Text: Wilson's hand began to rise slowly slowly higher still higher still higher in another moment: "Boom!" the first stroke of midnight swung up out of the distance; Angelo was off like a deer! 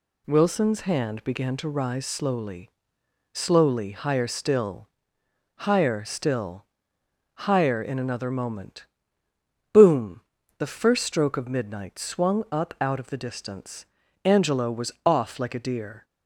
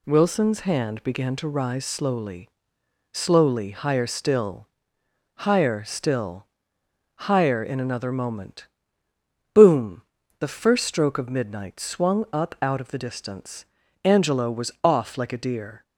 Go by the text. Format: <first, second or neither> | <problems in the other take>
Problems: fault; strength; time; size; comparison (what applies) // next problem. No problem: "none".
neither | pauses between "slowly" and "slowly"; noticeable; the same in both // pauses between "still" and "higher"; noticeable; the same in both // pauses between "still" and "higher"; noticeable; the same in both